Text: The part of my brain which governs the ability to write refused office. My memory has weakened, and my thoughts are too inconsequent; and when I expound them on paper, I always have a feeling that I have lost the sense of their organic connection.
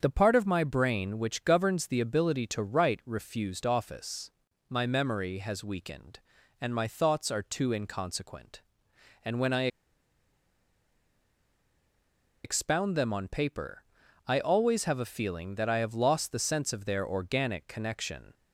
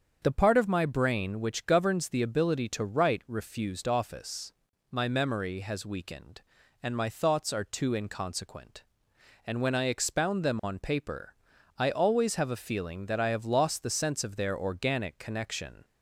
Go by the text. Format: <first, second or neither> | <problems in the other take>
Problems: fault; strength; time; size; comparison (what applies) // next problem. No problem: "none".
second | starts louder than the rest; strong; until 1.0 s; 7.5 dB; strong in the second // pauses between "I" and "expound"; strong; at 9.6 s; 2.7 s long